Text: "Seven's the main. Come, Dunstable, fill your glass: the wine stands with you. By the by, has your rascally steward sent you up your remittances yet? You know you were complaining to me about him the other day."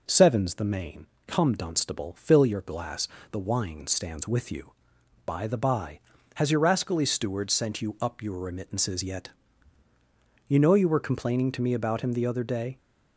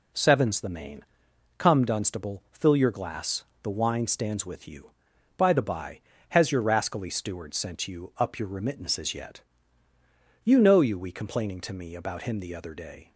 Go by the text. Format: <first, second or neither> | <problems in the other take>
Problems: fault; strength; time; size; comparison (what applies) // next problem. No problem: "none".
first | says "we" for "were"; at 10.9 s